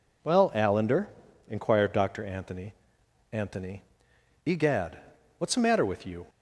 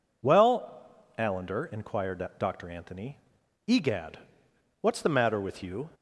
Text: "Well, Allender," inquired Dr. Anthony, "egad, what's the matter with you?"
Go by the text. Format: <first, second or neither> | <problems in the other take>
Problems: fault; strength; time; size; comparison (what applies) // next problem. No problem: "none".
second | says "Anthony" twice; at 3.3 s